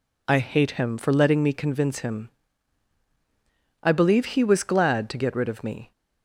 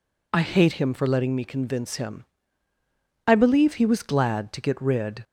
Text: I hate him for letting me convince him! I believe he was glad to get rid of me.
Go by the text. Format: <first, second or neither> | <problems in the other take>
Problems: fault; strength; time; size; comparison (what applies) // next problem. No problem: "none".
first | stops before "of me"; at 5.2 s